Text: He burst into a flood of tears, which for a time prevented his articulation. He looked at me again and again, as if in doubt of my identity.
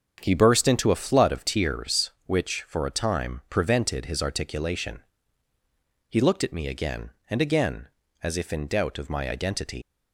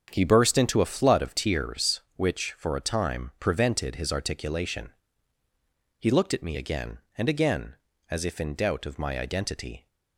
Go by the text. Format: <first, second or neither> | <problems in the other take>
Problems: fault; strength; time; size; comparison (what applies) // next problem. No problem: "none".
second | starts louder than the rest; until 1.2 s; 7 dB; strong in the second // leaves "identity" unfinished; at 9.8 s; 145 ms